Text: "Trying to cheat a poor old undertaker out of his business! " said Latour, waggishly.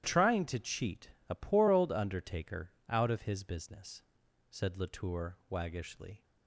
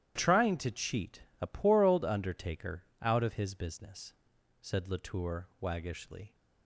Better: neither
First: starts louder than the rest; strong; until 1.3 s; 12 dB // pauses between "cheat" and "a"; slight; at 1.0 s; 0.22 s long // pauses between "undertaker" and "out"; slight; at 2.7 s; 0.18 s long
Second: starts louder than the rest; strong; until 1.4 s; 12 dB // pauses between "cheat" and "a"; slight; at 1.2 s; 0.22 s long // pauses between "undertaker" and "out"; slight; at 2.8 s; 0.18 s long

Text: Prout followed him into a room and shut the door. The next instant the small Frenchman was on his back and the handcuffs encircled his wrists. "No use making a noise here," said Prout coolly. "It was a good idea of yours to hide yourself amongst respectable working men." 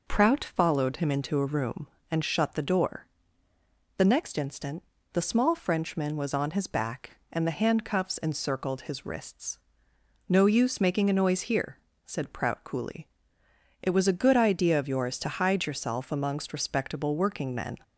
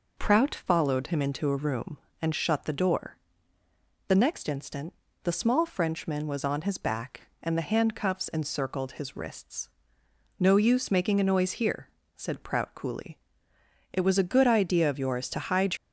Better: first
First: pauses between "instant" and "the"; slight; at 4.8 s; 0.30 s long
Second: pauses between "instant" and "the"; slight; at 4.9 s; 0.30 s long // stops before "yourself amongst respectable working men"; at 15.7 s

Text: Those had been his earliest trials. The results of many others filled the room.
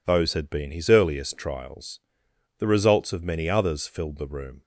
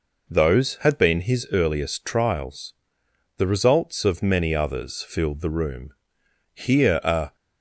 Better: first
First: none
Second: goes on to say "Here a"; noticeable; from 6.5 s on; 0.82 s long

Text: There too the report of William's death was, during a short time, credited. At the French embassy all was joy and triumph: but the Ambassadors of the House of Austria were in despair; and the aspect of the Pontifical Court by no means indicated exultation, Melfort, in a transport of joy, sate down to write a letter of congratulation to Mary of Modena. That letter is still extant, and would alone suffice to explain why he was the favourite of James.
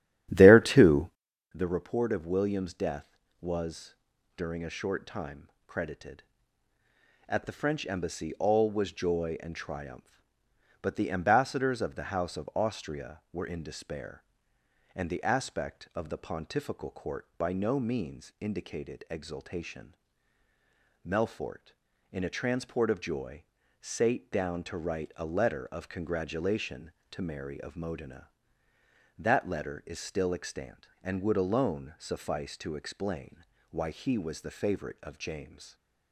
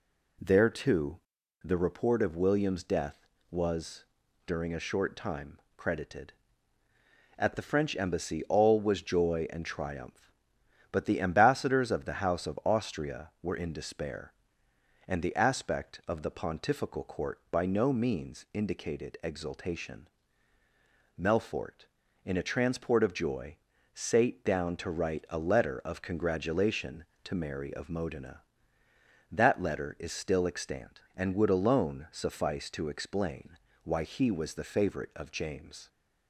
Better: second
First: starts louder than the rest; strong; until 1.2 s; 12 dB // pauses between "too" and "the"; noticeable; at 1.0 s; 0.46 s long // pauses between "explain" and "why"; slight; at 33.4 s; 0.28 s long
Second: pauses between "too" and "the"; noticeable; at 1.1 s; 0.46 s long // pauses between "explain" and "why"; slight; at 33.5 s; 0.28 s long

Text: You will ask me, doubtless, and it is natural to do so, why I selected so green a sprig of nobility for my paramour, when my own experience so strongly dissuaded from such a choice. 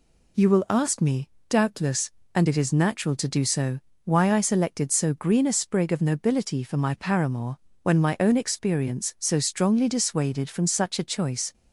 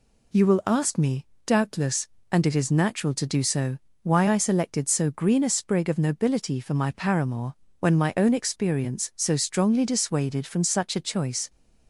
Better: neither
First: none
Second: none

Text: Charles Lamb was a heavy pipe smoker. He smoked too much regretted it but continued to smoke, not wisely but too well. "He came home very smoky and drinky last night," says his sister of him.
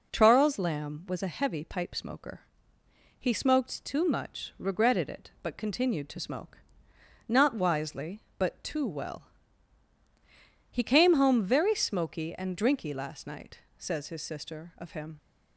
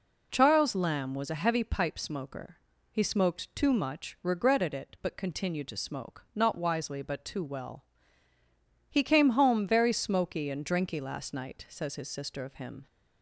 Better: neither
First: none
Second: none

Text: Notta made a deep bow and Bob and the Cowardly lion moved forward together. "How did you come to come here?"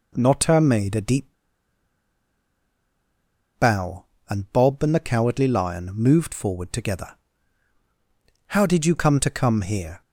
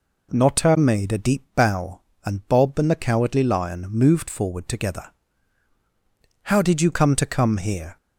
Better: second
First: pauses between "deep" and "bow"; strong; at 1.2 s; 2.3 s long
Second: none

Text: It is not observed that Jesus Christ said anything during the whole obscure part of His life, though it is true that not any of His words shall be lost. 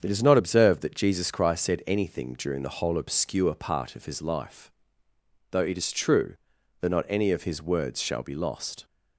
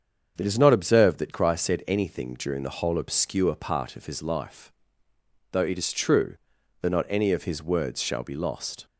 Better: first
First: starts louder than the rest; strong; until 1.0 s; 7.5 dB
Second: starts louder than the rest; strong; until 1.4 s; 7.5 dB // skips "Jesus"; at 1.3 s

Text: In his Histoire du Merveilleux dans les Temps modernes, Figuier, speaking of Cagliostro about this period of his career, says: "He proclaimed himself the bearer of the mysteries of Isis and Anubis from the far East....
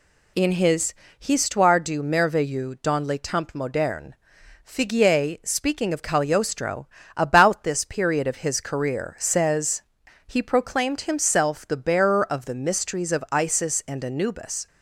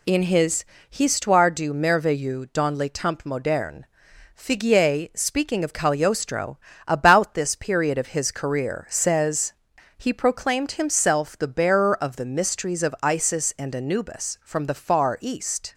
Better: second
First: pauses between "his" and "Histoire"; slight; at 0.9 s; 0.28 s long // pauses between "Cagliostro" and "about"; slight; at 6.8 s; 0.30 s long // stops before "from the far East"; at 14.6 s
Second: pauses between "his" and "Histoire"; slight; at 0.6 s; 0.28 s long // pauses between "Cagliostro" and "about"; slight; at 6.5 s; 0.30 s long

